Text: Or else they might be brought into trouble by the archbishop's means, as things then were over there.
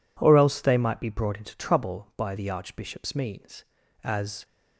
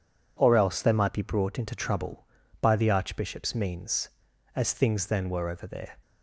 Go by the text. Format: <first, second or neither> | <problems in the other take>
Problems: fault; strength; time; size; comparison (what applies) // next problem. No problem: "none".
second | stops before "things then were over there"; at 4.4 s